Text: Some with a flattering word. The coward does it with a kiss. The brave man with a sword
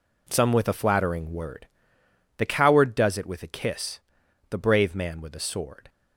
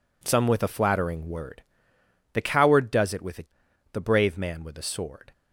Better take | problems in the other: first | skips "kiss"; at 3.6 s

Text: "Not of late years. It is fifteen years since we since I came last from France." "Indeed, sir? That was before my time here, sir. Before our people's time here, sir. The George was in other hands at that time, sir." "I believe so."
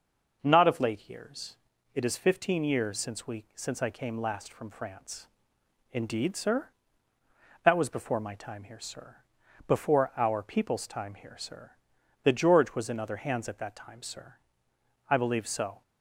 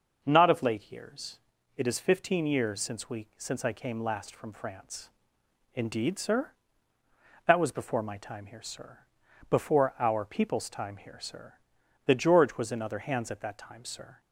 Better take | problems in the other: first | stops before "I believe so"; at 14.1 s

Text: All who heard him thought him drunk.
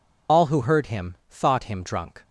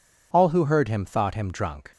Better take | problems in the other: second | loses the start of "All"; at 0.2 s; 50 ms // pauses between "him" and "thought"; slight; at 1.1 s; 0.16 s long

